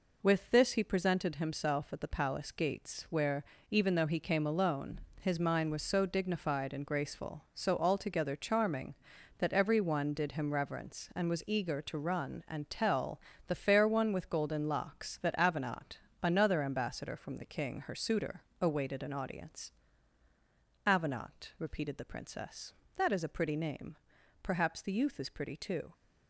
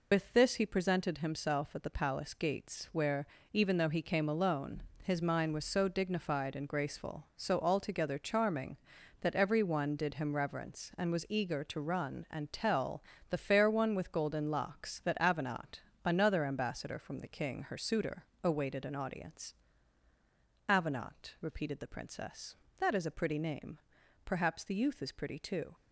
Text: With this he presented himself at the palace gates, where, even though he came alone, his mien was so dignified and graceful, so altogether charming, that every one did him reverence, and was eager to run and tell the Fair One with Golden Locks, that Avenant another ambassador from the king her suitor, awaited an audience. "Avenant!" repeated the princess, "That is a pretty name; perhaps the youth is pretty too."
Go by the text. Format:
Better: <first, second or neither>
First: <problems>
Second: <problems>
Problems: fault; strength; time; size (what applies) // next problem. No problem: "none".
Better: first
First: pauses between "tell" and "the"; slight; at 13.2 s; 0.26 s long // pauses between "Avenant" and "another"; slight; at 15.9 s; 0.22 s long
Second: loses the start of "With"; at 0.1 s; 70 ms // pauses between "tell" and "the"; slight; at 13.0 s; 0.26 s long // pauses between "Avenant" and "another"; slight; at 15.8 s; 0.22 s long